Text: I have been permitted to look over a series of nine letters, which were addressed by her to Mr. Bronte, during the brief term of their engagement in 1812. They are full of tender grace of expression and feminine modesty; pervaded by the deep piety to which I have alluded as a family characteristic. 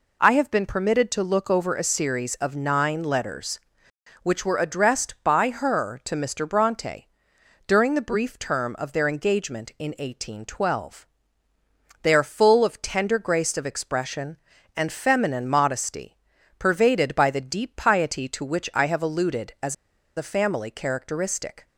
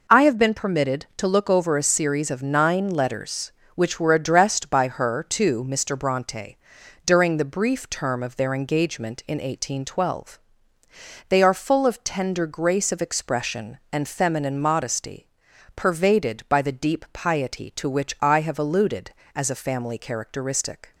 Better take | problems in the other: second | pauses between "as" and "a"; at 19.7 s; 0.41 s long

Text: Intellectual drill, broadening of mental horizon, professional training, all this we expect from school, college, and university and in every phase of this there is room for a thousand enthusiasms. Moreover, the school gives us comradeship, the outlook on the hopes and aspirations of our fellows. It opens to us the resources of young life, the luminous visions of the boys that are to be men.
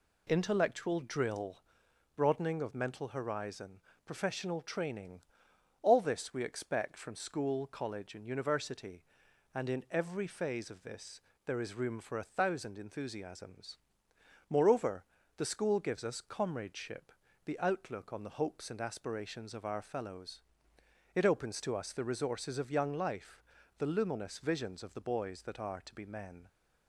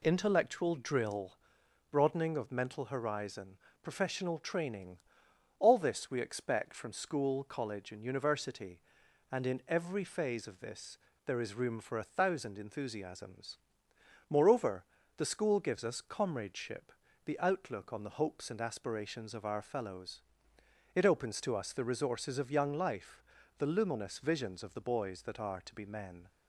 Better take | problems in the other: neither | pauses between "this" and "there"; slight; the same in both

